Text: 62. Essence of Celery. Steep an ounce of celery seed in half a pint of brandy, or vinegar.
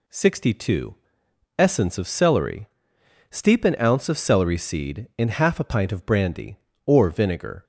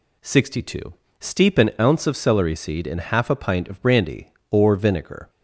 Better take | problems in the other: first | skips "Essence of Celery"; at 1.0 s

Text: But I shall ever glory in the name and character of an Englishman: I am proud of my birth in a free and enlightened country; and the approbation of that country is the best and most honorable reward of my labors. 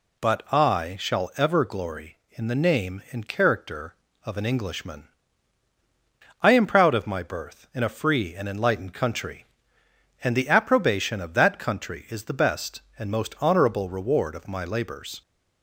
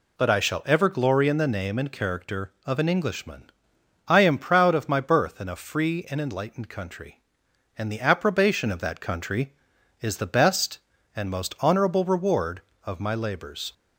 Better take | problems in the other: neither | none

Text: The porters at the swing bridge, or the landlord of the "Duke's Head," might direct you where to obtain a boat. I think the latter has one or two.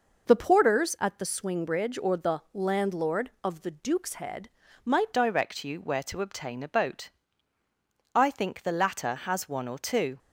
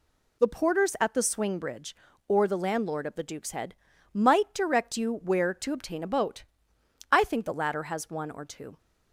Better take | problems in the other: second | changes voice at "direct"; from 5.1 s on; 5.0 s long

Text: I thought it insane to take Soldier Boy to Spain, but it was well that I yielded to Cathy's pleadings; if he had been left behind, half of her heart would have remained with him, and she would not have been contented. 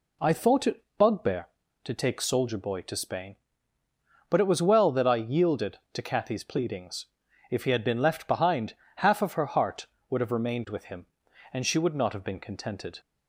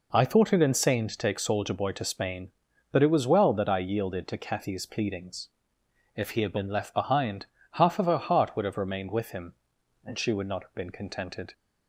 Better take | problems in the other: second | says "bugbear" for "insane"; at 0.9 s

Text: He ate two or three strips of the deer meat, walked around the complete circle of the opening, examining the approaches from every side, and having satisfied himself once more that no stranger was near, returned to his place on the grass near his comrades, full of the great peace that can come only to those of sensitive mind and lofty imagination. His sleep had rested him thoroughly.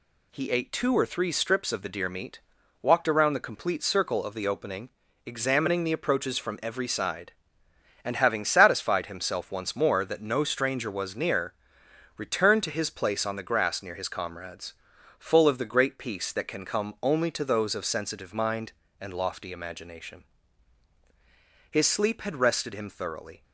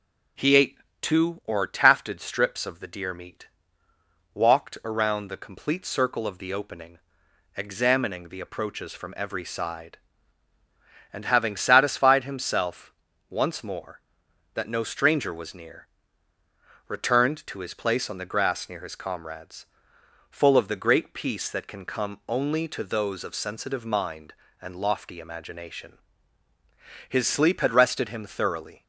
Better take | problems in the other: first | pauses between "ate" and "two"; slight; at 0.7 s; 0.24 s long // says "tafted" for "three"; at 1.6 s // pauses between "himself" and "once"; at 12.9 s; 0.38 s long

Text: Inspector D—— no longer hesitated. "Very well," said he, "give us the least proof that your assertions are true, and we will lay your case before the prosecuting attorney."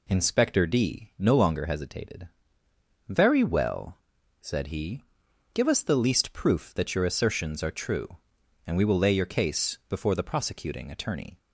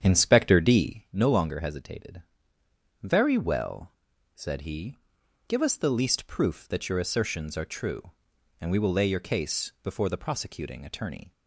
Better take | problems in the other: first | starts louder than the rest; strong; until 1.1 s; 8 dB

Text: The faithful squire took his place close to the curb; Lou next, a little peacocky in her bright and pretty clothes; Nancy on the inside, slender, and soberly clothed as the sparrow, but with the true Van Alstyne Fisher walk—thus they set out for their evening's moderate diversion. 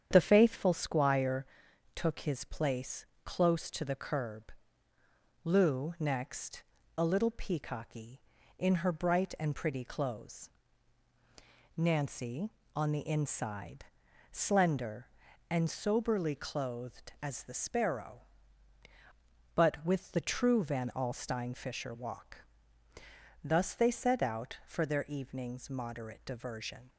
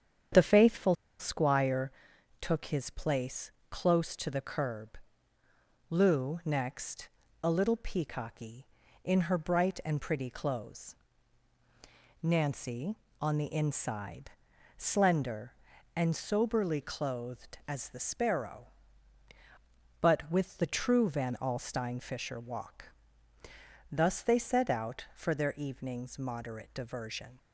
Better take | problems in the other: first | starts louder than the rest; strong; until 1.5 s; 8.5 dB; strong in the first // pauses between "faithful" and "squire"; slight; at 0.9 s; 0.24 s long // pauses between "squire" and "took"; noticeable; at 1.9 s; 0.50 s long; noticeable in the first // pauses between "place" and "close"; slight; at 3.5 s; 0.18 s long; slight in the first

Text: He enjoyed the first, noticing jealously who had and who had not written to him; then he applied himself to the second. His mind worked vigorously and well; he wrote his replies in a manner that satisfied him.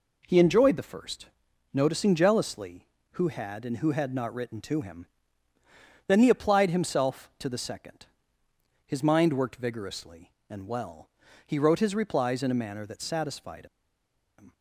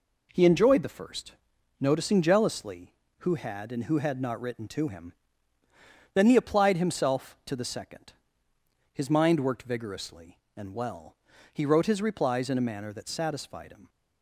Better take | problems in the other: second | pauses between "satisfied" and "him"; noticeable; at 13.6 s; 0.72 s long

